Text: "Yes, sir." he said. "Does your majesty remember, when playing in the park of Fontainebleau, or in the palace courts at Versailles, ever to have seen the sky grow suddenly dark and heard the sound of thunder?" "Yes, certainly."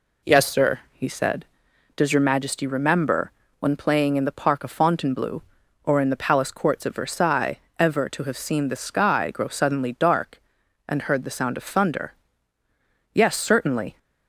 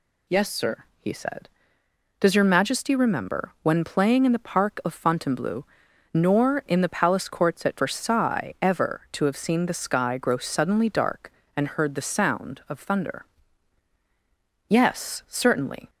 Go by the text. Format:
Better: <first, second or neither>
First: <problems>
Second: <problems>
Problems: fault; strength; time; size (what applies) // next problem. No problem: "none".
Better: first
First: none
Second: says "nor" for "or"; at 6.1 s